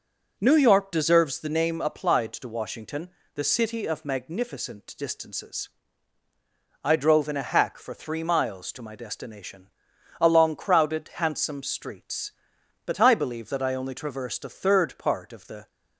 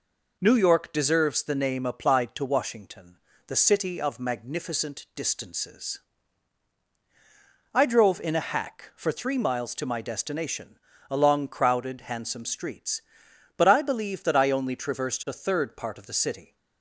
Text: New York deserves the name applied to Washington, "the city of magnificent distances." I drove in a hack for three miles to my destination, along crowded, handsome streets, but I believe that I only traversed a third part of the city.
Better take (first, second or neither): second